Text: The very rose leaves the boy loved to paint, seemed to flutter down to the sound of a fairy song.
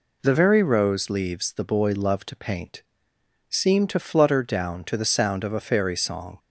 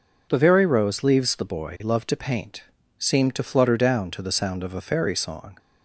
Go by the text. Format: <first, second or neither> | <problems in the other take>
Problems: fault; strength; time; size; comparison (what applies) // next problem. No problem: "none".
neither | none